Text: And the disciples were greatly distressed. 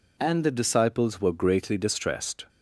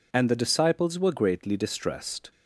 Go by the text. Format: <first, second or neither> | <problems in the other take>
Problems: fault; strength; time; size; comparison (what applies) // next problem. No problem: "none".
neither | none